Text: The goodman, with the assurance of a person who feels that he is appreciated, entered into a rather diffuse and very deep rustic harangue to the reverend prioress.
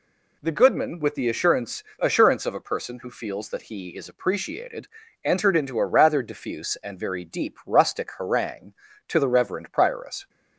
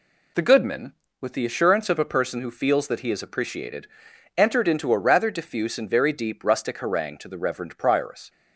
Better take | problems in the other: second | says "assurance" twice; at 1.9 s

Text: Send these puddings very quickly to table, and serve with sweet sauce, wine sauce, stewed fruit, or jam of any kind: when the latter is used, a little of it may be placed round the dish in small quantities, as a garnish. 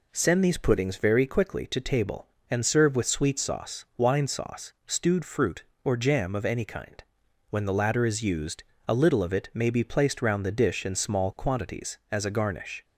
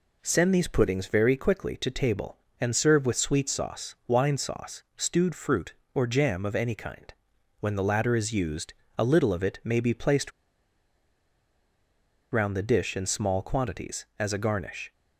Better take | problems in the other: first | pauses between "placed" and "round"; strong; at 10.3 s; 2.0 s long

